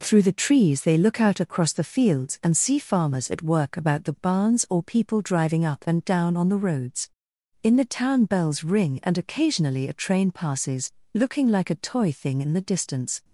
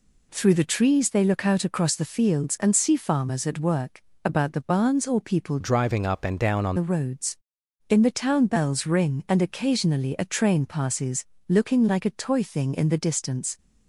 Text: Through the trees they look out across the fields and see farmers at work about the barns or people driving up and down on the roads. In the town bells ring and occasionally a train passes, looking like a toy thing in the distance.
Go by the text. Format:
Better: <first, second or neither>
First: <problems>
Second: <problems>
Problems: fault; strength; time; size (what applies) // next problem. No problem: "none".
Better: first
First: none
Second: pauses between "work" and "about"; slight; at 4.0 s; 0.22 s long // changes voice from "driving" to "on"; from 5.6 to 6.7 s; 1.1 s long